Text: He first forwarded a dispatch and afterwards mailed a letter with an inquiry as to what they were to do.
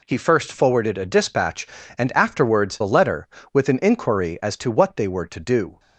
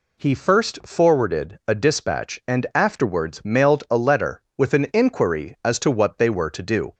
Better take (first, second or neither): second